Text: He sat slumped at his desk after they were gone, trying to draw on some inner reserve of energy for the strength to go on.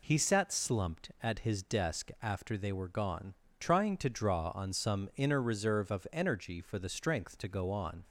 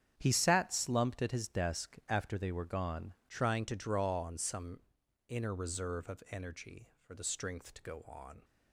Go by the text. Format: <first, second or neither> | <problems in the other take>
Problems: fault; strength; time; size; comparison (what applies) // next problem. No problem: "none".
first | starts louder than the rest; strong; until 1.1 s; 9 dB // changes voice at "trying"; from 3.2 s on; 5.2 s long // pauses between "some" and "inner"; noticeable; at 4.8 s; 0.48 s long